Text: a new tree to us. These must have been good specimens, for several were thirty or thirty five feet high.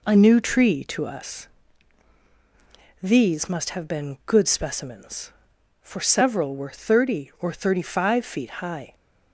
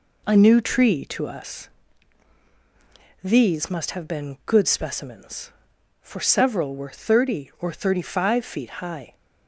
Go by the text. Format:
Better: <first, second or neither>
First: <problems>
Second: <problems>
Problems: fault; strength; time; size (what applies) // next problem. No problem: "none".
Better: neither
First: none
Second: none